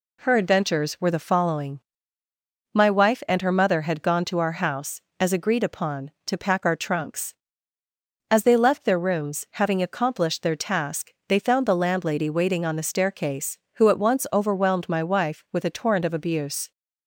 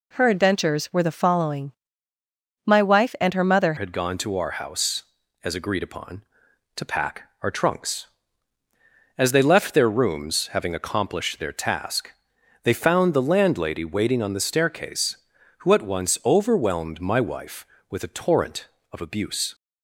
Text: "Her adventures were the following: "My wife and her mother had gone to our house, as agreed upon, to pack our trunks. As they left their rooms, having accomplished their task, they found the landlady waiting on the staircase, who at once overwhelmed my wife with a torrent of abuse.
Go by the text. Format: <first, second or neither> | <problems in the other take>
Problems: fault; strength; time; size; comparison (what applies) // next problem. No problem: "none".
first | changes voice at "had"; from 3.7 s on; 15.8 s long